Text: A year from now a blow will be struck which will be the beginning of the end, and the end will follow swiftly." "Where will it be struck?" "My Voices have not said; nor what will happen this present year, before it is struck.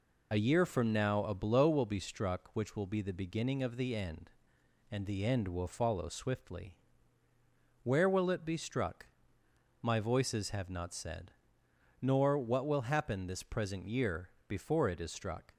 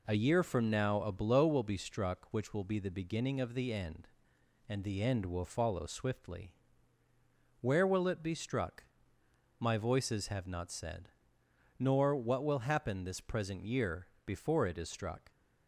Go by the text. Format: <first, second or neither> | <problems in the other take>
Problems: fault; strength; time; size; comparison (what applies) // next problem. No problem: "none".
second | loses the start of "A"; at 0.3 s; 30 ms